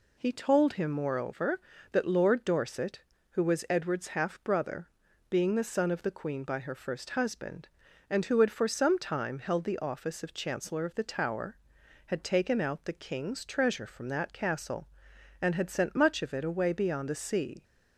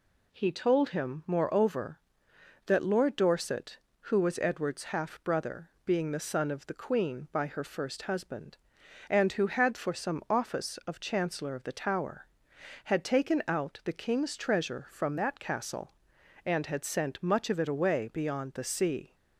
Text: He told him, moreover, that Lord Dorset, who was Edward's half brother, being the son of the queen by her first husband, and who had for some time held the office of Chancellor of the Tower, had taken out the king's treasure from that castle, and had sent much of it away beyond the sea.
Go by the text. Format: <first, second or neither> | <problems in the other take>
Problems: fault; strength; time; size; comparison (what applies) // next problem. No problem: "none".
first | skips "time held the"; at 10.2 s